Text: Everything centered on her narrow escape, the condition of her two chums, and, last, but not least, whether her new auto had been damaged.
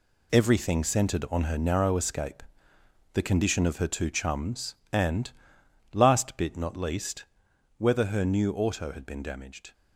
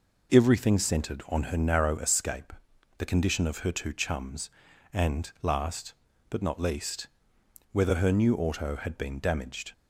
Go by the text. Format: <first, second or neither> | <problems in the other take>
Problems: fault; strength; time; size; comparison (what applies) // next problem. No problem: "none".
second | says "bit" for "but"; at 6.3 s